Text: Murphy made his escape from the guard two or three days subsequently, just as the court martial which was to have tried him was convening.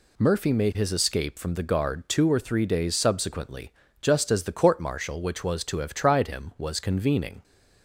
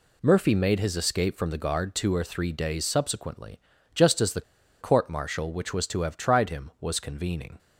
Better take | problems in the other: first | pauses between "the" and "court"; at 4.4 s; 0.39 s long

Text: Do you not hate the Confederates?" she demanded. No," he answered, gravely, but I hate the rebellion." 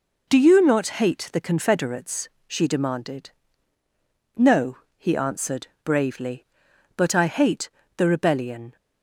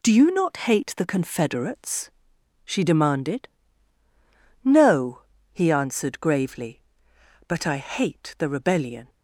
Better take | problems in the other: second | says "bravely" for "gravely"; at 5.8 s // pauses between "hate" and "the"; slight; at 7.6 s; 0.26 s long

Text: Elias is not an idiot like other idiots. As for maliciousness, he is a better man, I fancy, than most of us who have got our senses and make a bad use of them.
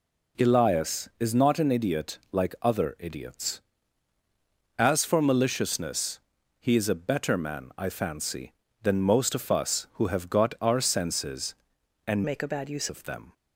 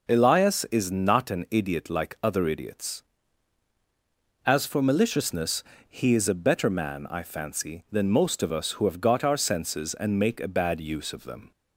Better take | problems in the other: second | changes voice from "make" to "use"; from 12.2 to 12.8 s; 0.6 s long

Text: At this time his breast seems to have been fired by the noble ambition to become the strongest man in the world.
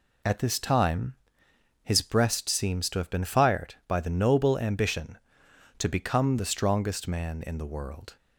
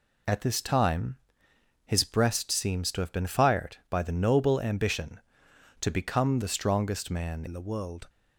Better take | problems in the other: first | pauses between "time" and "his"; noticeable; at 1.1 s; 0.68 s long; noticeable in the first // changes voice at "in"; from 7.4 s on; 0.6 s long

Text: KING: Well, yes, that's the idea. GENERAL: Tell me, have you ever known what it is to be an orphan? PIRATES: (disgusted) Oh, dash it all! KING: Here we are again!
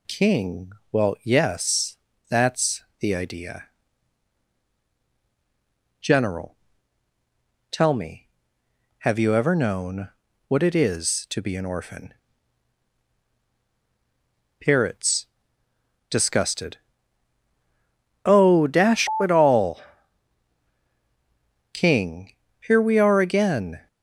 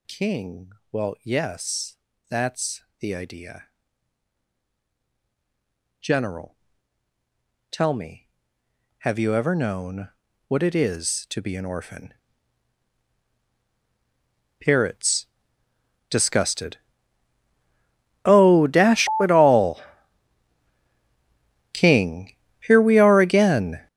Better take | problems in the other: first | gets louder; strong; throughout; 14 dB // pauses between "that's" and "the"; slight; at 2.8 s; 0.16 s long; slight in the first // pauses between "known" and "what"; at 10.0 s; 0.38 s long; also in the first

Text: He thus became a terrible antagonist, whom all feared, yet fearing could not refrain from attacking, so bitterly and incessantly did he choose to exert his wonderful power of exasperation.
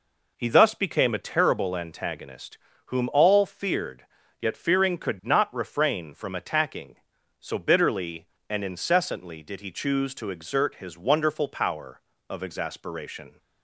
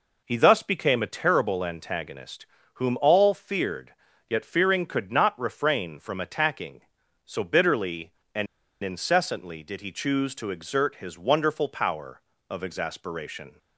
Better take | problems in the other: first | pauses between "and" and "incessantly"; at 8.4 s; 0.37 s long

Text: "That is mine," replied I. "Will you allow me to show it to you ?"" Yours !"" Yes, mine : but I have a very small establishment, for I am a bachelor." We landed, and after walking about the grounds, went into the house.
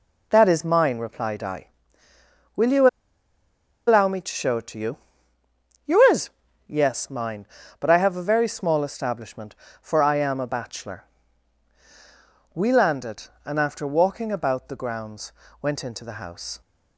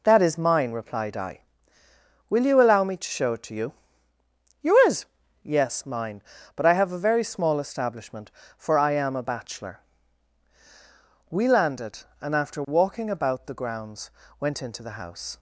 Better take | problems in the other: second | pauses between "you" and "allow"; at 2.8 s; 1.0 s long

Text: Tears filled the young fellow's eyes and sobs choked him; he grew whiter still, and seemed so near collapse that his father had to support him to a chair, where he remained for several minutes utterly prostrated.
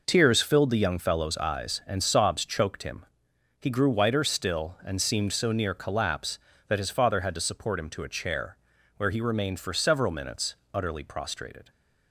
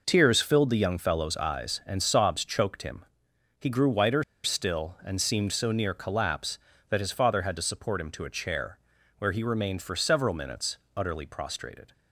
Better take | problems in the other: first | pauses between "whiter" and "still"; slight; at 4.2 s; 0.20 s long // pauses between "minutes" and "utterly"; slight; at 10.7 s; 0.20 s long; slight in the first

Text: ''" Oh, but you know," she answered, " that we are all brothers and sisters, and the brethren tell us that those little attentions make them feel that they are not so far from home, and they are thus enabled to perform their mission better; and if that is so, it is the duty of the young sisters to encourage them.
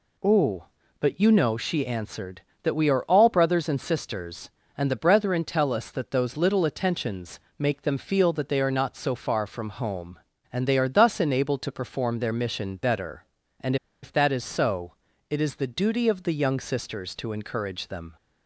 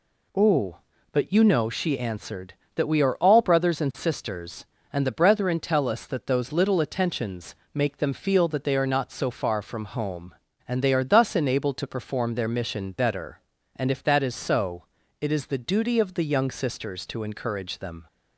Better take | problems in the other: second | pauses between "attentions" and "make"; slight; at 7.3 s; 0.20 s long; slight in the second // pauses between "and" and "if"; slight; at 13.7 s; 0.27 s long

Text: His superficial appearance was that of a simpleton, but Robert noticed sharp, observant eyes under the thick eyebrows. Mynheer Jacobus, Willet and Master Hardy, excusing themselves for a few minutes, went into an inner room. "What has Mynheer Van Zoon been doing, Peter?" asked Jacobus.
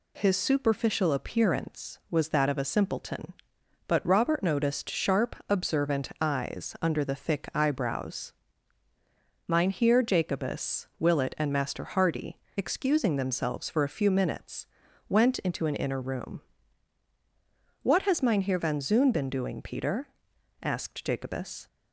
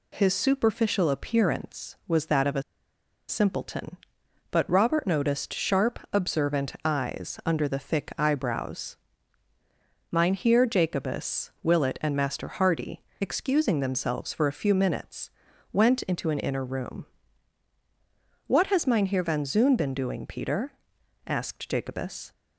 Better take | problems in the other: first | pauses between "a" and "simpleton"; noticeable; at 2.6 s; 0.67 s long

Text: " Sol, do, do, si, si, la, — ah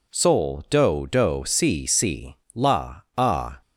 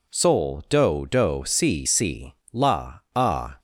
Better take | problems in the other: neither | none

